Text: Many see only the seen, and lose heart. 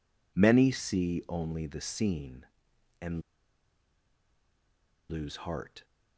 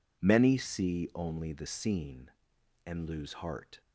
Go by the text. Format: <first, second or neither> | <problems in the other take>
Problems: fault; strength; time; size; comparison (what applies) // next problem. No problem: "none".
second | pauses between "and" and "lose"; strong; at 3.2 s; 1.8 s long